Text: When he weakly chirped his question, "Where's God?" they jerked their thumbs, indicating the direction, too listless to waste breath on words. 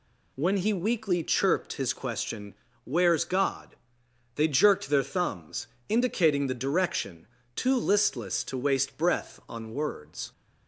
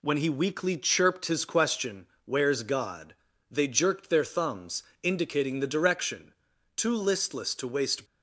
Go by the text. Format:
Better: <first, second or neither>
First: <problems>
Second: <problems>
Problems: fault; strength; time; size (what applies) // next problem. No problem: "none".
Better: first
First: none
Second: stops before "breath on words"; at 8.0 s